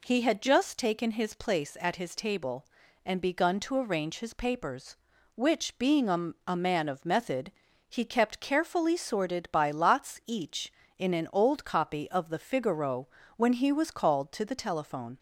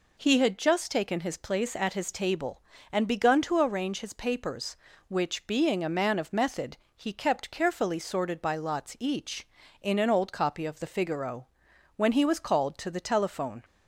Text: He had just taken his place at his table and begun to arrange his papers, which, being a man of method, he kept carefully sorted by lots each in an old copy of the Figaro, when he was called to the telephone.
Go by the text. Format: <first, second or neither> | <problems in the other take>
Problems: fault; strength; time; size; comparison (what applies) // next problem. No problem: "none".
second | says "a" twice; at 6.4 s